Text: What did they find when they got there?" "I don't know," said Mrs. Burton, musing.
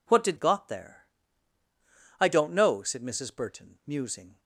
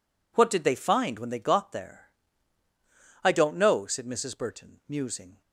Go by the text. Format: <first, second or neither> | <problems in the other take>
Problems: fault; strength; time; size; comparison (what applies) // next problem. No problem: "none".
second | skips "they find when they"; at 0.3 s